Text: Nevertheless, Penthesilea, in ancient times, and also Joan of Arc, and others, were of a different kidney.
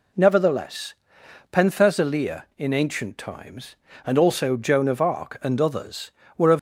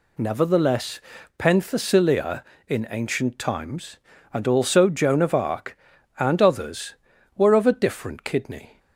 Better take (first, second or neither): second